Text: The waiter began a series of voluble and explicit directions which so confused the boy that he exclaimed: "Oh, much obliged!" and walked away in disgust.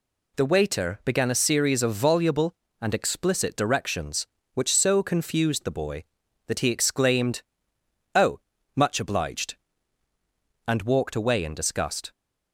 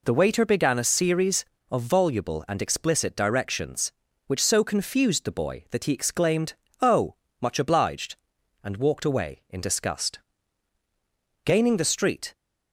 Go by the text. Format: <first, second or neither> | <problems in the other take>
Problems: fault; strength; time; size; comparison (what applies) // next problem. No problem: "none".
first | goes on to say "Gaining the street"; noticeable; from 11.4 s on; 0.90 s long